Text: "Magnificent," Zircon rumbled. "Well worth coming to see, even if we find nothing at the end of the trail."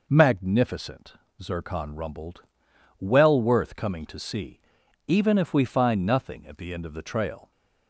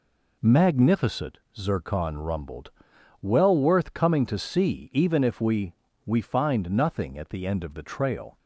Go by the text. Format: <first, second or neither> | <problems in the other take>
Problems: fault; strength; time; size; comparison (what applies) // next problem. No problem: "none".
first | says "we" twice; at 6.0 s